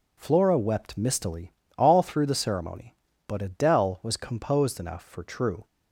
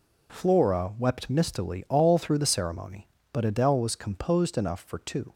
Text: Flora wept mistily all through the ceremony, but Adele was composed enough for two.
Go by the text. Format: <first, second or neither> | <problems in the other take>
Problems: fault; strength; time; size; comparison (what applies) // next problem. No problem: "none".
second | pauses between "mistily" and "all"; slight; at 1.5 s; 0.26 s long // says "true" for "two"; at 5.2 s